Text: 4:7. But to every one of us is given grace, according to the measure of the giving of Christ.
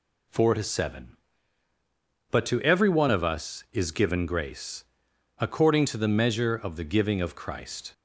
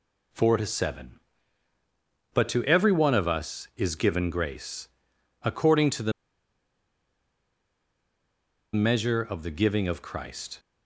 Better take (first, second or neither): first